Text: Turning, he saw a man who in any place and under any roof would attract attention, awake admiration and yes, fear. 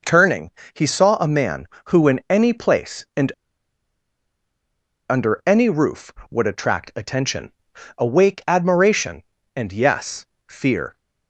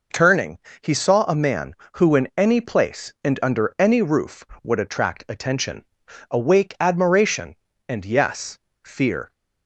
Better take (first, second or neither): second